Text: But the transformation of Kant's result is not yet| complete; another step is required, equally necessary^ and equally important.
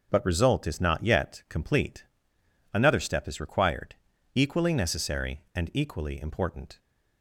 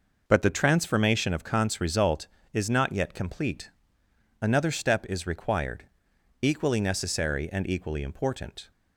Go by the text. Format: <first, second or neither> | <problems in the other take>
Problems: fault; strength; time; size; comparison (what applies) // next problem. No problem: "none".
second | skips "the transformation of Kant's"; at 0.2 s